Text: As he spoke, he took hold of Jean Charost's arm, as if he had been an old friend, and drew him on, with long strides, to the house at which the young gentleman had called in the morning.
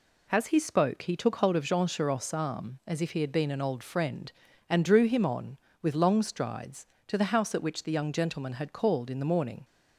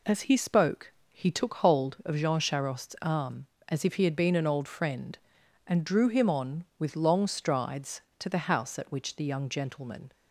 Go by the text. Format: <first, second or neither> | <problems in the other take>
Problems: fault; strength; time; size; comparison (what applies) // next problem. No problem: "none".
first | stops before "had called in the morning"; at 10.1 s